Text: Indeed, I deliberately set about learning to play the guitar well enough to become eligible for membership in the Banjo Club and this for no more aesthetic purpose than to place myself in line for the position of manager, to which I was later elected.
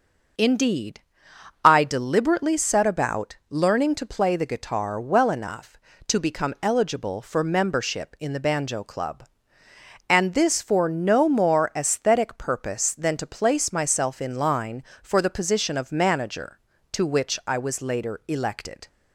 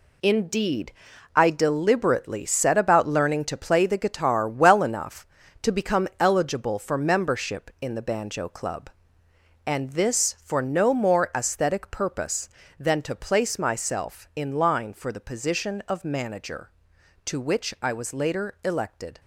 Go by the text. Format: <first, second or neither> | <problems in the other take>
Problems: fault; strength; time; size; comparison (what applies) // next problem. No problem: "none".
first | gets quieter; strong; throughout; 8.5 dB